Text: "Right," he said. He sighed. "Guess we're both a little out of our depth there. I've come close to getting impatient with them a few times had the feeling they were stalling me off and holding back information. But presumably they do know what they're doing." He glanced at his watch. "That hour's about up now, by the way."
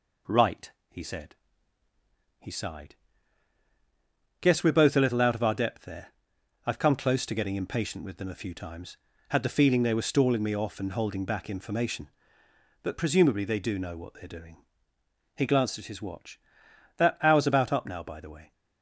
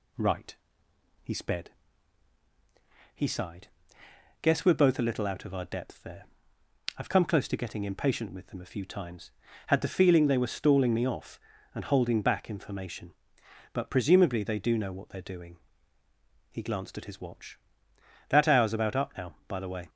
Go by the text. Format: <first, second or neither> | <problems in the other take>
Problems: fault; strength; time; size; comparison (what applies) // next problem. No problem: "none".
first | says "sped" for "said"; at 1.3 s